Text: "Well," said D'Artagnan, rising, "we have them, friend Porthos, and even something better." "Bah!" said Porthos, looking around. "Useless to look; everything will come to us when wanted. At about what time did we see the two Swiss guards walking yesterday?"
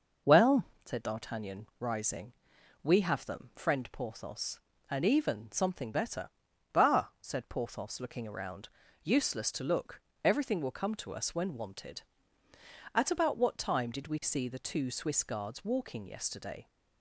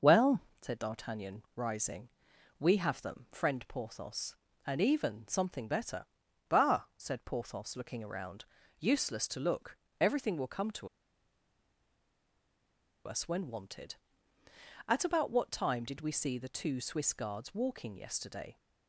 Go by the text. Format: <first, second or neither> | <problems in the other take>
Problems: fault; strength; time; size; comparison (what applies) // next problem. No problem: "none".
first | pauses between "to" and "us"; strong; at 10.8 s; 2.1 s long